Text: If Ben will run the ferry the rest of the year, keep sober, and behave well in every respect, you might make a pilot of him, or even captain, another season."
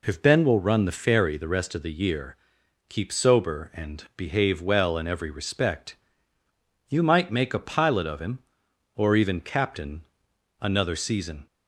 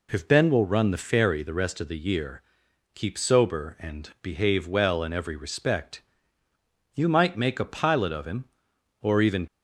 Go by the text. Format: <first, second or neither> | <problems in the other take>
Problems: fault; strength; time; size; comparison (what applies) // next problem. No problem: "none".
first | stops before "captain another season"; at 9.4 s